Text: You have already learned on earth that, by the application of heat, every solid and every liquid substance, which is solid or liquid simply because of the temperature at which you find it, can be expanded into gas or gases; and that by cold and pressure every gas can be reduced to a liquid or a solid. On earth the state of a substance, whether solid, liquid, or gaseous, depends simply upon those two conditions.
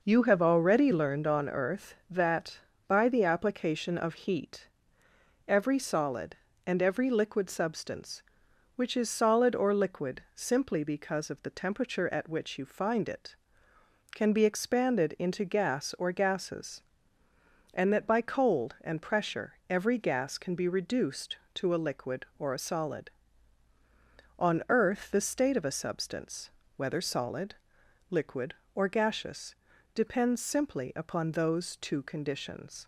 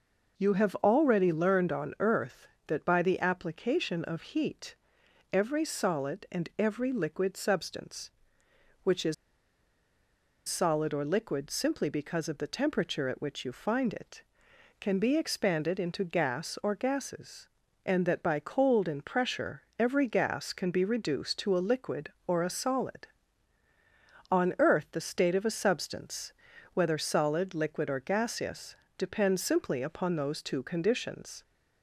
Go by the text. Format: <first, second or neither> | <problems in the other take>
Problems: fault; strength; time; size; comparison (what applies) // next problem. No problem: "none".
first | pauses between "is" and "solid"; strong; at 9.1 s; 1.3 s long